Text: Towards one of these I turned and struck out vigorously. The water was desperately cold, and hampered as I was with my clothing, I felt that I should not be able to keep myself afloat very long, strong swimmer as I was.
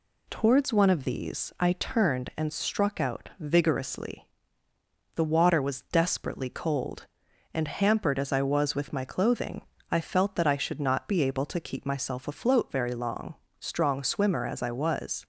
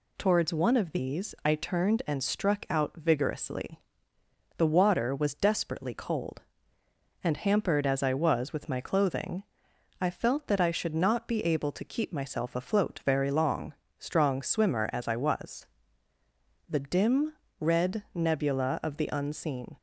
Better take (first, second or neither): first